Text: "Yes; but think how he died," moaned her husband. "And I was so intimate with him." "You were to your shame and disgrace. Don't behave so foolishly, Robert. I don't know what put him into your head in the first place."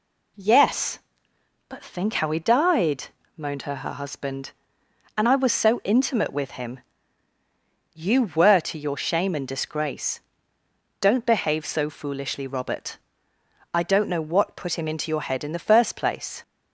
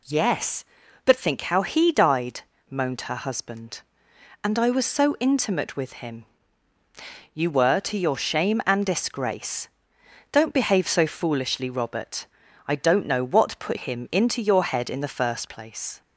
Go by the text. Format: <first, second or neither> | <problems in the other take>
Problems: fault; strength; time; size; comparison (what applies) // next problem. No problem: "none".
second | says "her" twice; at 3.7 s